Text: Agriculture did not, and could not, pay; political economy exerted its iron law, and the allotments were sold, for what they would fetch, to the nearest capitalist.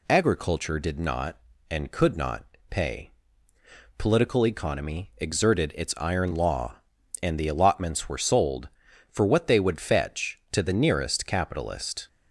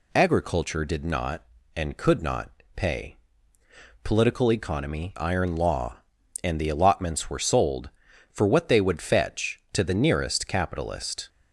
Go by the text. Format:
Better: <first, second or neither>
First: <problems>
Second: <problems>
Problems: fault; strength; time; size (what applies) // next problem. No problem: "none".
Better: first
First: none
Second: skips "exerted its"; at 5.1 s